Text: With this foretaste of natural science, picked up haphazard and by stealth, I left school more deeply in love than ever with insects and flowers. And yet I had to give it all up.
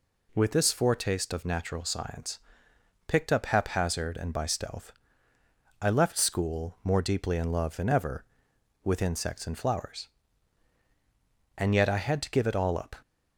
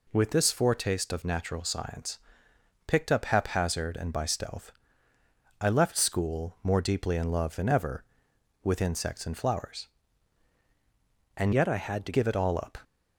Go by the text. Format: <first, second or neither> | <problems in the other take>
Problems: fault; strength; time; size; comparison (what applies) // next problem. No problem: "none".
first | changes voice from "yet" to "to"; from 11.5 to 12.1 s; 0.6 s long